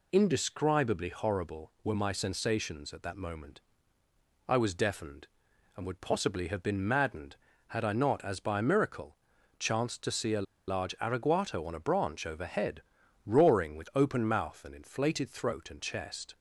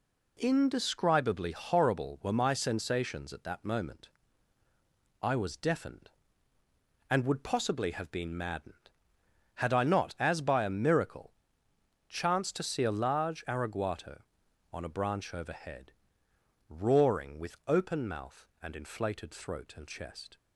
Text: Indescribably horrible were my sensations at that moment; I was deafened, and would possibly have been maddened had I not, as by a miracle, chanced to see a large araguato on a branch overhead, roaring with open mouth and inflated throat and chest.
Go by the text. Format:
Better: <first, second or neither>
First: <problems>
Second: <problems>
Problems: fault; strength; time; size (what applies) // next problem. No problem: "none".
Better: second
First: pauses between "a" and "large"; slight; at 10.4 s; 0.23 s long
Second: none